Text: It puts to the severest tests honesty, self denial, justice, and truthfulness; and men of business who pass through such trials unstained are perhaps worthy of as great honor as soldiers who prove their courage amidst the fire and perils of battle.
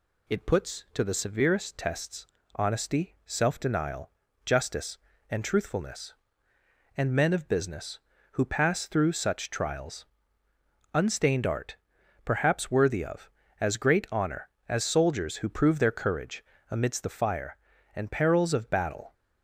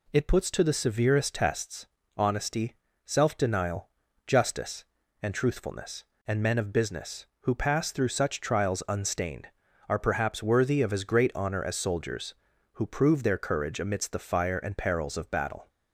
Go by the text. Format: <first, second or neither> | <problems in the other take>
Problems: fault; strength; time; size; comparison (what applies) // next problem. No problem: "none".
second | pauses between "tests" and "honesty"; slight; at 2.2 s; 0.30 s long; slight in the second // pauses between "trials" and "unstained"; noticeable; at 10.0 s; 0.88 s long // says "art" for "are"; at 11.4 s // pauses between "courage" and "amidst"; slight; at 16.4 s; 0.28 s long